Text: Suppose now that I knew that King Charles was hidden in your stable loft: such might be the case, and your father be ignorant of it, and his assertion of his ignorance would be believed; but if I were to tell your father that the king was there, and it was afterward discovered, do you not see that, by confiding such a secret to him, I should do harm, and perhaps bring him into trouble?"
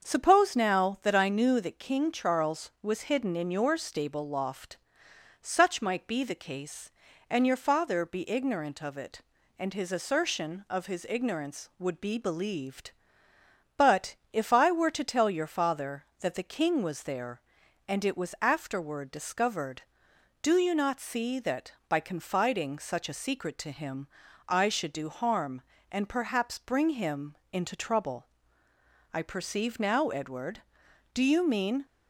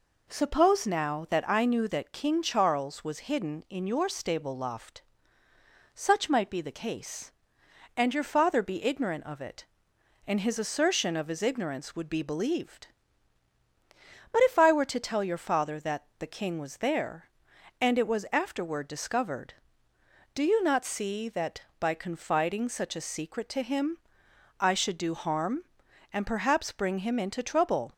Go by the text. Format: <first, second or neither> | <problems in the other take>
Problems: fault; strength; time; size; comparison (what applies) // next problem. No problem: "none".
second | starts louder than the rest; until 1.1 s; 7 dB // pauses between "but" and "if"; slight; at 14.1 s; 0.18 s long // pauses between "him" and "into"; slight; at 27.3 s; 0.16 s long // goes on to say "I perceive now Edward do you mean"; strong; from 29.1 s on; 2.7 s long